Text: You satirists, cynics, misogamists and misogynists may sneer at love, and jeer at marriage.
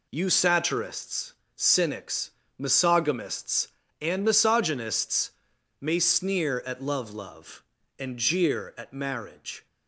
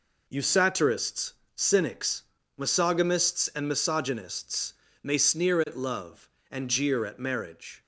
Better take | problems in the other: second | pauses between "misogynists" and "may"; noticeable; at 5.3 s; 0.50 s long; slight in the second // says "love" twice; at 7.1 s

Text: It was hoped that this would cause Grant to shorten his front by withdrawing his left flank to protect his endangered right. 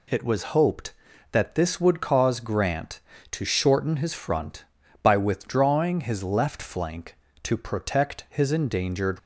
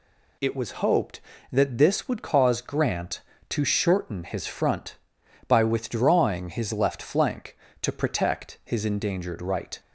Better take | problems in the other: second | stops before "right"; at 9.1 s

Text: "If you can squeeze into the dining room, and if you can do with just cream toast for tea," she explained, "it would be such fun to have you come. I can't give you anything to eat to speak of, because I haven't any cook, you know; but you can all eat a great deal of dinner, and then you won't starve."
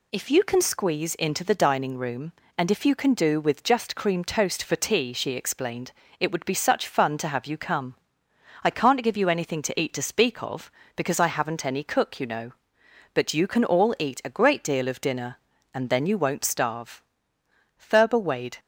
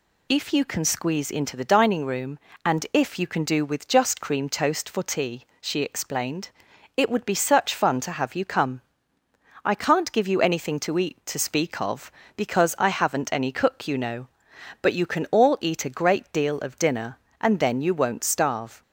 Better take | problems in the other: second | goes on to say "Thurber Wade"; noticeable; from 17.7 s on; 0.82 s long

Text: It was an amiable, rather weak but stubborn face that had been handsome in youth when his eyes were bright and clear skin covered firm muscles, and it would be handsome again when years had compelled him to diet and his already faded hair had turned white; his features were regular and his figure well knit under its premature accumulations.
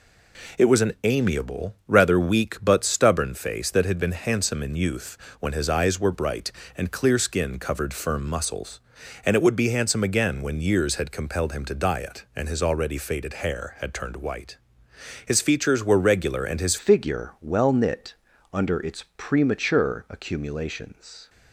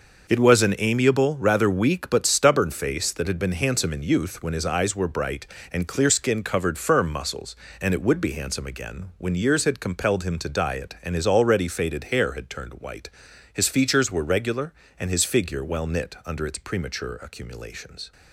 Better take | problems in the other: second | pauses between "youth" and "when"; slight; at 5.1 s; 0.24 s long // changes voice at "figure"; from 16.7 s on; 4.5 s long // pauses between "knit" and "under"; at 18.1 s; 0.40 s long

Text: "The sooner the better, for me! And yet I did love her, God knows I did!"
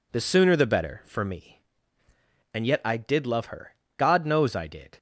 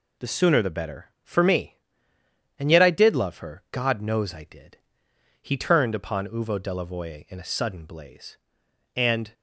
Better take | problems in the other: first | goes on to say "He turned upon Uvo Delavoye in a sudden blaze And"; strong; from 5.4 s on; 3.9 s long

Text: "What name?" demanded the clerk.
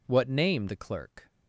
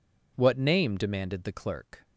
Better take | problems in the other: second | skips "demanded"; at 0.6 s

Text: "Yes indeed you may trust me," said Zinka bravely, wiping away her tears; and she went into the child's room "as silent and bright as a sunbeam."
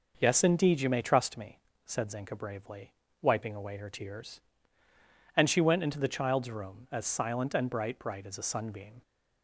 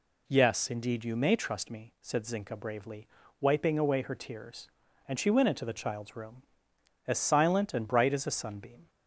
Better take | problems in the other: second | says "bright" twice; at 7.9 s

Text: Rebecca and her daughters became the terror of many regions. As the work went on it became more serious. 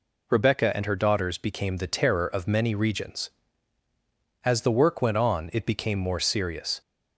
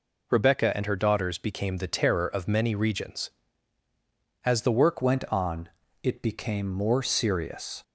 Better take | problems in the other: first | changes voice at "went"; from 5.0 s on; 2.8 s long // pauses between "on" and "it"; slight; at 5.6 s; 0.34 s long

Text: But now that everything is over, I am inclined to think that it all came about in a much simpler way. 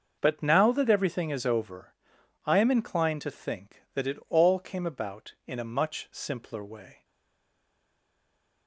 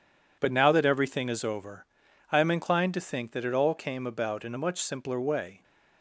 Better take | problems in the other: second | starts louder than the rest; until 1.2 s; 6.5 dB // stays silent after the last word; noticeable; from 7.0 s on; 1.6 s long

